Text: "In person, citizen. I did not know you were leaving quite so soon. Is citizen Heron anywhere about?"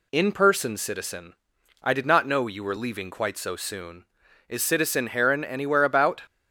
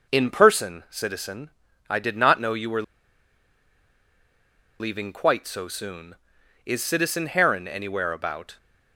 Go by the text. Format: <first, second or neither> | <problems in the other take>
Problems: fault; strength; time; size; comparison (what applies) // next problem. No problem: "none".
first | pauses between "were" and "leaving"; strong; at 2.8 s; 1.9 s long